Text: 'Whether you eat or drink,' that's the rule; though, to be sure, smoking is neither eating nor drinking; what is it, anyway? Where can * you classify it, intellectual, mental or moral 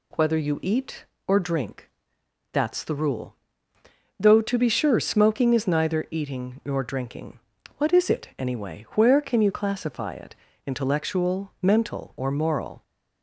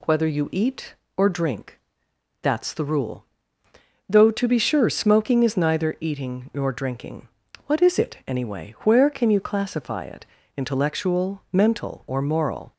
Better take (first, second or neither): neither